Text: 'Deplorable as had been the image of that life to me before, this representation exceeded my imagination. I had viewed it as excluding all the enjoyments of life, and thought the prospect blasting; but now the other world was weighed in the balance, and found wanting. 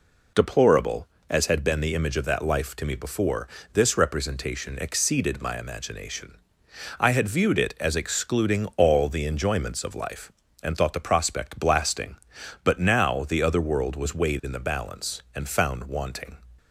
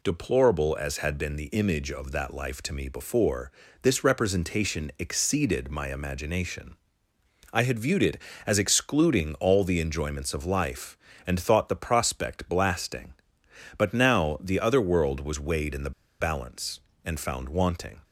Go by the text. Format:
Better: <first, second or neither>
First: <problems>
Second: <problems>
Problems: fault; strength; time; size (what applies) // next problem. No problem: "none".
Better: first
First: none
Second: pauses between "the" and "balance"; slight; at 15.9 s; 0.29 s long